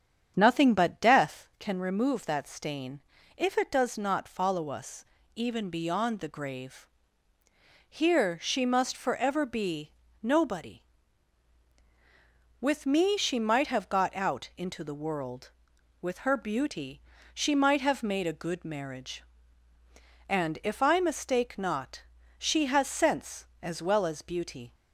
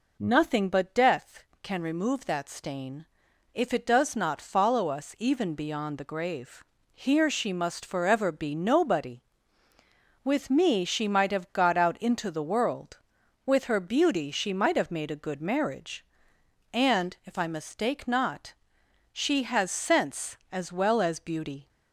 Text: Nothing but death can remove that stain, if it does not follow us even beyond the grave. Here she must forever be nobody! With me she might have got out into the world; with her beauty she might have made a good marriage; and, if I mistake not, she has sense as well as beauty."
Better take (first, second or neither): second